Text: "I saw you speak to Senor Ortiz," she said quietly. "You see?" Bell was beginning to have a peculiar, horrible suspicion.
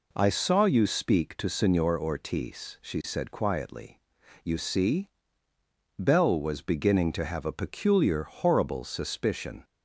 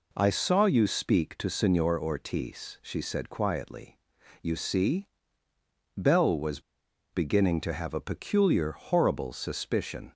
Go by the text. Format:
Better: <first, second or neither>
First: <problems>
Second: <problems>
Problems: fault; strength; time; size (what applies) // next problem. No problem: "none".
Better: first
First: none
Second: pauses between "was" and "beginning"; noticeable; at 6.6 s; 0.52 s long